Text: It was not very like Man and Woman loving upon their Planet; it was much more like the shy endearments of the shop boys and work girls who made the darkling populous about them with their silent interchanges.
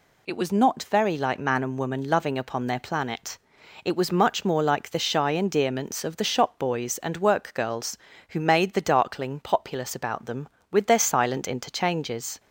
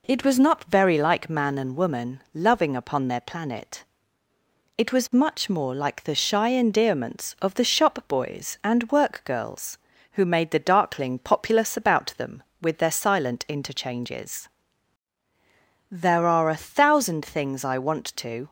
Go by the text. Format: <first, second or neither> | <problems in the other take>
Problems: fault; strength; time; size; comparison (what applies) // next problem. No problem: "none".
first | goes on to say "There are a thousand things I want to"; strong; from 15.9 s on; 2.5 s long